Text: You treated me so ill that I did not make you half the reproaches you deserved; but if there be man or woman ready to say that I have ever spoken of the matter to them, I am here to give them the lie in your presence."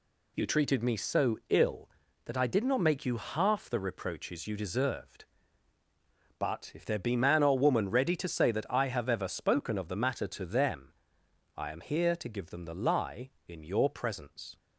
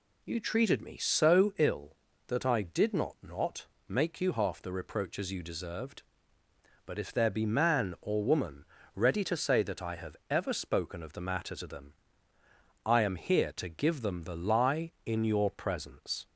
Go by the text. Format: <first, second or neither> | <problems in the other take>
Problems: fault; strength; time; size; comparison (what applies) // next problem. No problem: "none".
first | says "not" twice; at 3.2 s // pauses between "woman" and "ready"; slight; at 8.6 s; 0.31 s long